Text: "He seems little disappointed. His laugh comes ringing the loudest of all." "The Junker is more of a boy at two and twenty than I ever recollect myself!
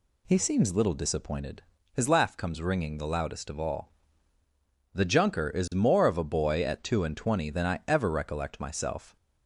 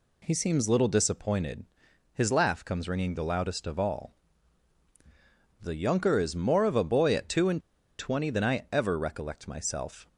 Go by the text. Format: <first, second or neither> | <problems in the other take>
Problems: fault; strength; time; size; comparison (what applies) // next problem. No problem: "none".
first | pauses between "and" and "twenty"; at 7.5 s; 0.39 s long